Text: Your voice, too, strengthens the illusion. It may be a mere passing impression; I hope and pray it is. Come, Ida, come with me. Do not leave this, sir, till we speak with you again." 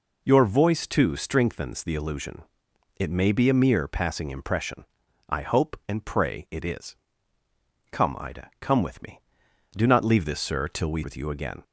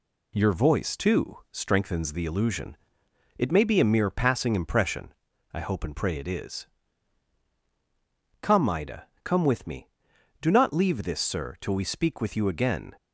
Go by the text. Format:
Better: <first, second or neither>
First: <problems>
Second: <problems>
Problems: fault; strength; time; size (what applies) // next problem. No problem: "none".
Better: second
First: skips "speak"; at 11.0 s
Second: none